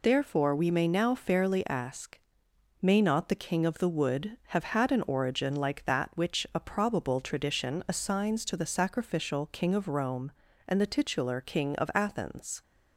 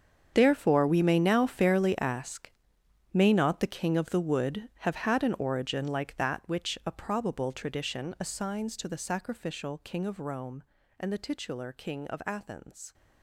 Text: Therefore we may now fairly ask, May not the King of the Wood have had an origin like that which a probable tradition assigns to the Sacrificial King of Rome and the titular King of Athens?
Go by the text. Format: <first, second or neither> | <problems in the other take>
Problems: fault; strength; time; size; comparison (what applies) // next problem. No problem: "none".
first | gets quieter; strong; throughout; 15 dB